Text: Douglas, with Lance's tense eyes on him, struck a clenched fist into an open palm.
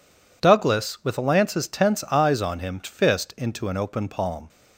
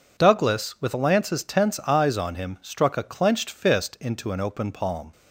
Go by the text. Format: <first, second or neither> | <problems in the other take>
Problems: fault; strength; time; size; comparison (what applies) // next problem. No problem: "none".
second | skips "struck a clenched"; at 2.8 s